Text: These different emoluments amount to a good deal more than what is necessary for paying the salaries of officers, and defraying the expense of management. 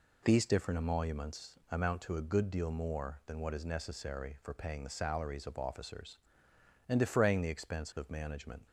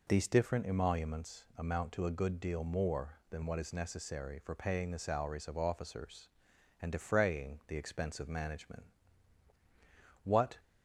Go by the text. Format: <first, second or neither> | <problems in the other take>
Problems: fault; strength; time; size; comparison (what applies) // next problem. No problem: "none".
first | goes on to say "What"; slight; from 10.2 s on; 0.36 s long